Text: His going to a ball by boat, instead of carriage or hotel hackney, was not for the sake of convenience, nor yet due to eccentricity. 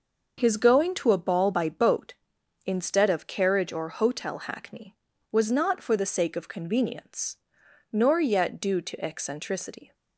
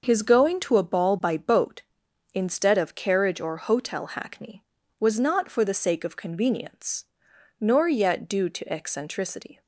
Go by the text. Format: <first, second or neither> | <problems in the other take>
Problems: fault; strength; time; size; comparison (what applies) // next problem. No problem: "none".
neither | starts louder than the rest; noticeable; the same in both